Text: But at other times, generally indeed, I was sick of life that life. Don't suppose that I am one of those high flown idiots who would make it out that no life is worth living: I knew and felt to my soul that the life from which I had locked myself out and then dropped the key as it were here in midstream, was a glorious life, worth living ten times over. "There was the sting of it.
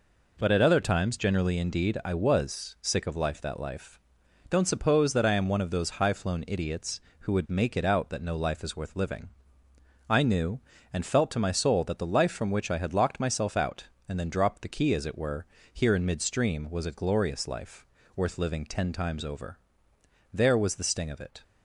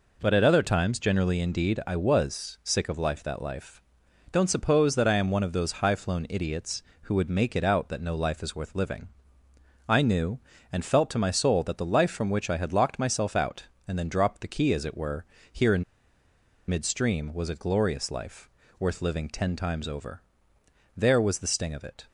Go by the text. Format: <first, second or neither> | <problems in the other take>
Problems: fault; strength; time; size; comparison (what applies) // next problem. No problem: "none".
first | pauses between "were" and "here"; slight; at 15.2 s; 0.26 s long; slight in the first // pauses between "in" and "midstream"; noticeable; at 15.8 s; 0.86 s long